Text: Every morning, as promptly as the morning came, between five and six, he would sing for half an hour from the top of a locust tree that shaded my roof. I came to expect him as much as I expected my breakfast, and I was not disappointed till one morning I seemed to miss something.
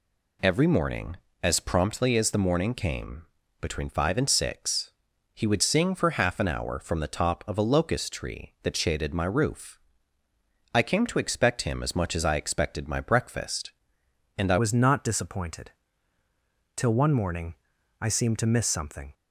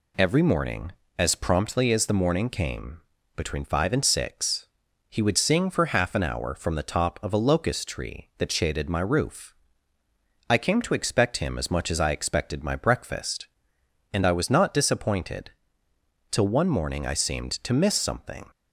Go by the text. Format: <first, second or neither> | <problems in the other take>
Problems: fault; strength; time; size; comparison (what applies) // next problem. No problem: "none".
second | changes voice at "was"; from 14.5 s on; 4.6 s long // pauses between "disappointed" and "till"; at 15.6 s; 1.0 s long; noticeable in the second // pauses between "morning" and "I"; noticeable; at 17.5 s; 0.48 s long